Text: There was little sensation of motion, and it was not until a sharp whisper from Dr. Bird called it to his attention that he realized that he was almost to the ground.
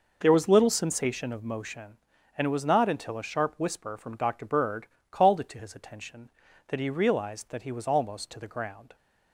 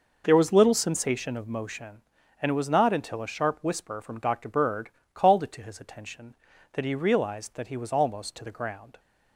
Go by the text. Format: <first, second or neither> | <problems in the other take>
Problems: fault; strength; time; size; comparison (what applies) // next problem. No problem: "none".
neither | pauses between "Bird" and "called"; slight; the same in both